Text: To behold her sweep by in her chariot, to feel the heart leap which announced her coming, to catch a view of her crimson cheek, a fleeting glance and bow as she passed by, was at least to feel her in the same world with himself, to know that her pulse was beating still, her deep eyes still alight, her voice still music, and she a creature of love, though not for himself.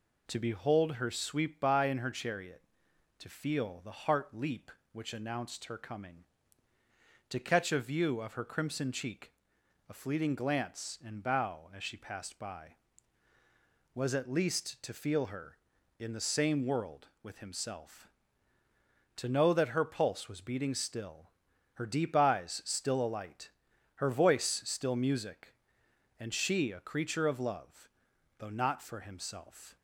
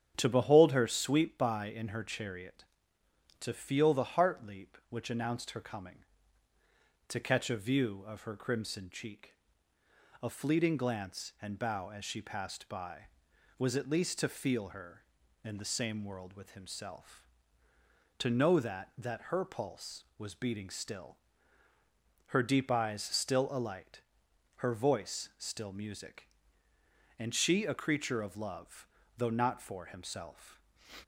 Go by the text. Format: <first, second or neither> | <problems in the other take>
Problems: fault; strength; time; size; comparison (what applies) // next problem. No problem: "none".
first | starts louder than the rest; strong; until 1.1 s; 9 dB // says "that" twice; at 18.9 s